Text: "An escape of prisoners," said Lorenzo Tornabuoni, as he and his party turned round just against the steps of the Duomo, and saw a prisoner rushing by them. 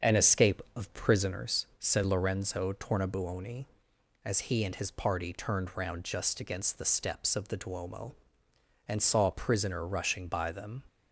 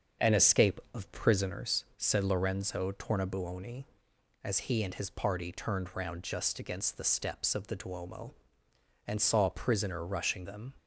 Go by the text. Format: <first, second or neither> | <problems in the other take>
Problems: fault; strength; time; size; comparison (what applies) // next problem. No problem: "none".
first | starts louder than the rest; until 1.3 s; 7 dB; also in the first // skips "by"; at 10.4 s